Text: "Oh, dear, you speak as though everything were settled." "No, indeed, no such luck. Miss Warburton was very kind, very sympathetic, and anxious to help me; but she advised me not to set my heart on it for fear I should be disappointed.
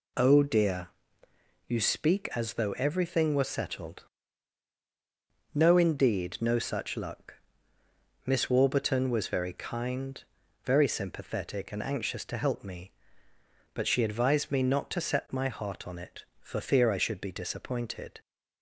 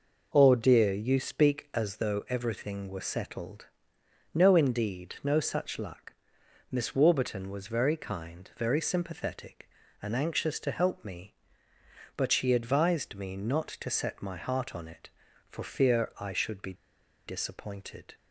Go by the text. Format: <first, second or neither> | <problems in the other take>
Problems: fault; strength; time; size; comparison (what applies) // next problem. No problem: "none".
first | pauses between "be" and "disappointed"; noticeable; at 16.7 s; 0.53 s long